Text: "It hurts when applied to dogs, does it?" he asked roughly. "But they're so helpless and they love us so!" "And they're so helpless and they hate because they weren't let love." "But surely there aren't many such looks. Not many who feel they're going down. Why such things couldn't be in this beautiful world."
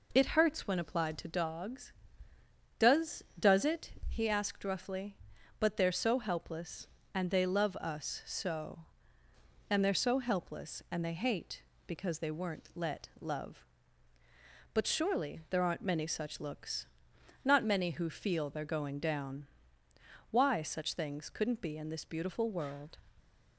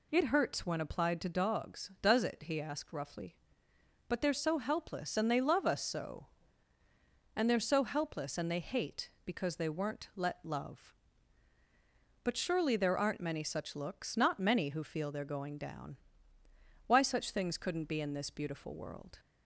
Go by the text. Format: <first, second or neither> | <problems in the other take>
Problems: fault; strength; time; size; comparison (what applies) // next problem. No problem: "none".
second | says "does" twice; at 3.3 s